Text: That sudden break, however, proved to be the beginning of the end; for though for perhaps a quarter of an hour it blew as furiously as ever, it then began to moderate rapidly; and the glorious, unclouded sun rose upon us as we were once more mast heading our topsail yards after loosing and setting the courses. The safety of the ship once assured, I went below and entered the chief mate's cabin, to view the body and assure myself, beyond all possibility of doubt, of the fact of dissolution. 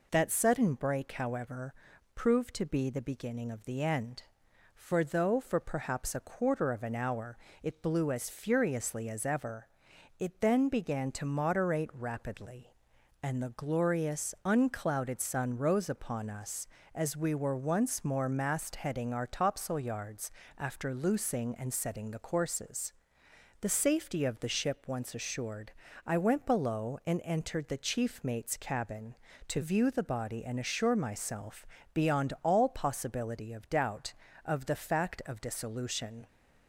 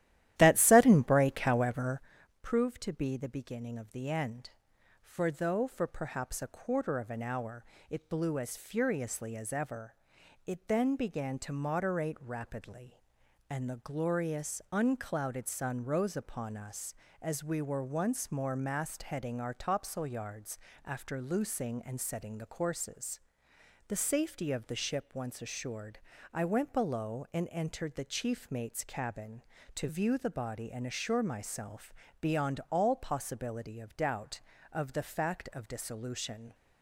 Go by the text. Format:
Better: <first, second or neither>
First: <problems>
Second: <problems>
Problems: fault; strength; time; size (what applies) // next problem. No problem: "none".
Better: first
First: pauses between "hour" and "it"; slight; at 7.3 s; 0.24 s long // pauses between "yards" and "after"; slight; at 20.3 s; 0.26 s long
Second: starts louder than the rest; strong; until 2.1 s; 13 dB // pauses between "hour" and "it"; slight; at 7.6 s; 0.24 s long // pauses between "yards" and "after"; slight; at 20.5 s; 0.26 s long